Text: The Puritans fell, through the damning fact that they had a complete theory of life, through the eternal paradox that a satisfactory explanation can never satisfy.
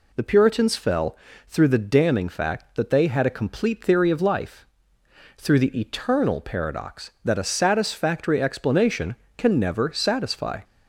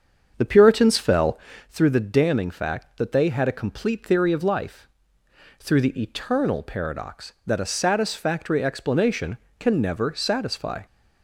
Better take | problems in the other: first | starts louder than the rest; strong; until 1.7 s; 7 dB

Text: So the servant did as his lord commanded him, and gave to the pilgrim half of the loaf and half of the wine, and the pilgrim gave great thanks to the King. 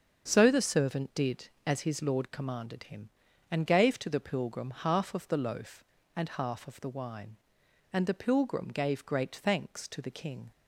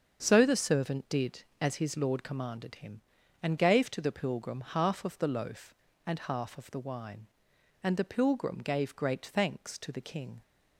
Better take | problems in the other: neither | starts louder than the rest; the same in both

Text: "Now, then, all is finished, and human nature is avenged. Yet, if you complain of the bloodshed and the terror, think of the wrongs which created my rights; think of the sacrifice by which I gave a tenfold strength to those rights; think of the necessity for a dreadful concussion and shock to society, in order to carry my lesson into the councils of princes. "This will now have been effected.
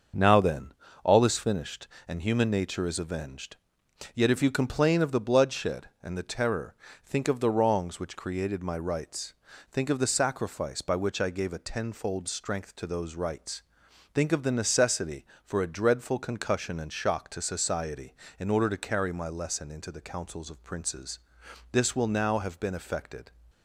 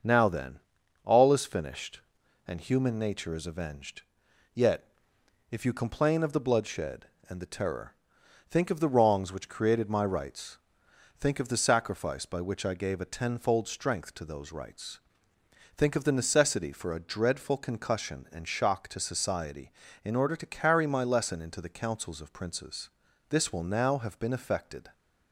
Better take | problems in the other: neither | starts louder than the rest; the same in both

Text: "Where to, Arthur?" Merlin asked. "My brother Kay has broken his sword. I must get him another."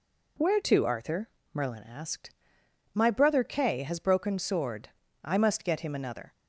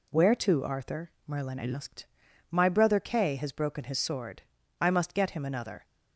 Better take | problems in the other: second | skips "his"; at 4.3 s

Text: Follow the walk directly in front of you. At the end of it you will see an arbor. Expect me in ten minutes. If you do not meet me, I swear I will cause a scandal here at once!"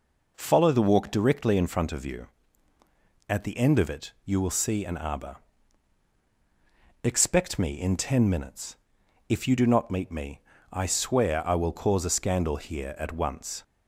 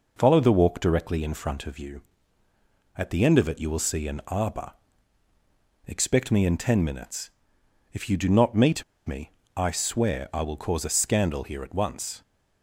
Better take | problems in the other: first | pauses between "meet" and "me"; slight; at 8.8 s; 0.23 s long

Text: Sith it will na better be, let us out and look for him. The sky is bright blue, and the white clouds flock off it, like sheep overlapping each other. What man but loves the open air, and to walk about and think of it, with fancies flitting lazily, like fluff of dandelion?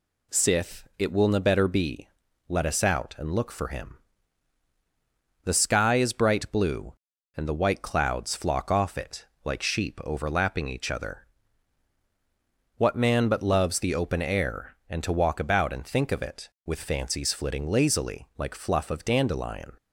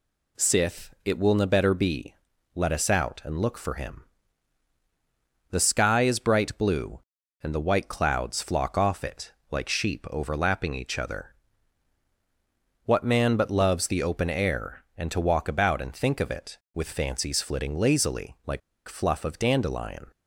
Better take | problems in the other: first | pauses between "like" and "fluff"; slight; at 18.6 s; 0.28 s long

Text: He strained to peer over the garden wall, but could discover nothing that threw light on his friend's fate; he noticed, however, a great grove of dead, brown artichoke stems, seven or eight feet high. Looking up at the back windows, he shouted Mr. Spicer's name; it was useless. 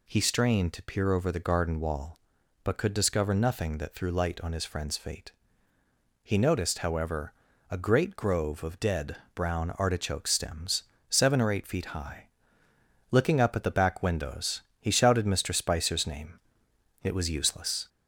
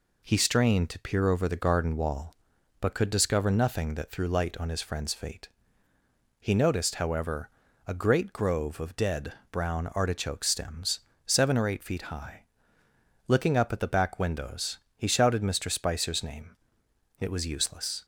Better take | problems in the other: second | gets louder; slight; throughout; 2.5 dB

